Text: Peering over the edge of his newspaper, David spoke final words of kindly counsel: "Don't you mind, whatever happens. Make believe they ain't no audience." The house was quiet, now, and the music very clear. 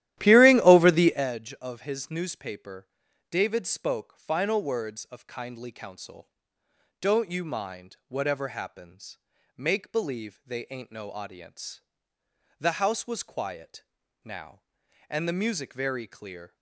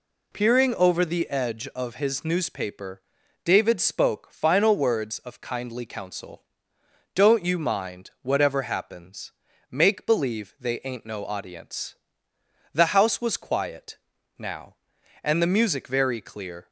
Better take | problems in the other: second | starts louder than the rest; strong; until 1.3 s; 13.5 dB

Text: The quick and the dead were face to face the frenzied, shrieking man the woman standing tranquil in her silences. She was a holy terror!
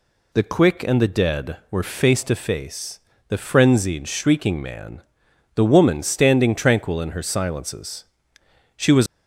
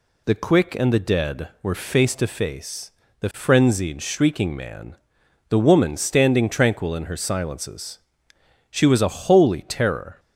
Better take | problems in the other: second | pauses between "face" and "the"; slight; at 2.9 s; 0.28 s long; slight in the second // pauses between "man" and "the"; noticeable; at 5.0 s; 0.50 s long; noticeable in the second // stops before "a holy terror"; at 9.0 s

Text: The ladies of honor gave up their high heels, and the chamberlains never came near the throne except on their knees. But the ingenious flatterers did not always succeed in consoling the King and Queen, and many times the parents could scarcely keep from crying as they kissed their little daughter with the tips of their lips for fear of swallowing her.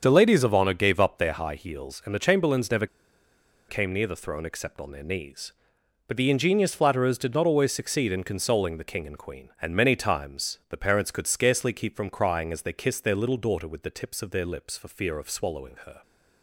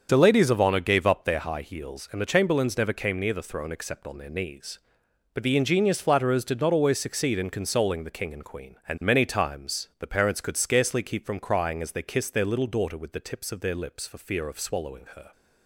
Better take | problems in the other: second | starts louder than the rest; strong; until 1.0 s; 7 dB; also in the second // pauses between "never" and "came"; noticeable; at 2.8 s; 0.82 s long

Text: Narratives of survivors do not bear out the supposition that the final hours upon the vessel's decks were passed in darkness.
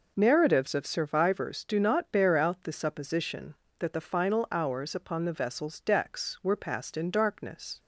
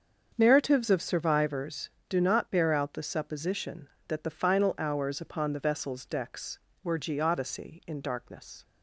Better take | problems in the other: first | starts louder than the rest; until 1.3 s; 7 dB // says "geodesy" for "passed"; at 6.9 s

